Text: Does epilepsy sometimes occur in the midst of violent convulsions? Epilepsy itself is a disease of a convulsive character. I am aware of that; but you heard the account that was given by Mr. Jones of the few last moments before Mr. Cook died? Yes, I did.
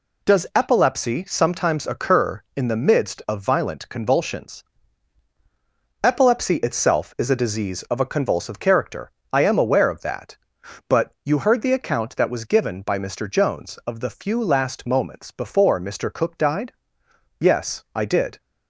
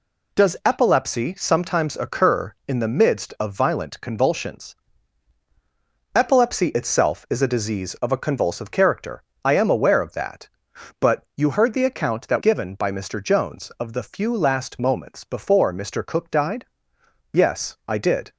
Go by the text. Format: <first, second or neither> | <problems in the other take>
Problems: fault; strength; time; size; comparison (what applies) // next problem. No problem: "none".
first | skips "was"; at 12.3 s